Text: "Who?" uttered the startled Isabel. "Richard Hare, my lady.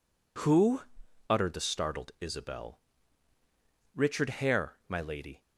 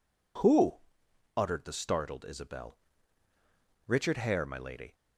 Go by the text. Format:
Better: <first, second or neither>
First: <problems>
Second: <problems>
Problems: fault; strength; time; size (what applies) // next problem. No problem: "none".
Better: neither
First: none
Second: none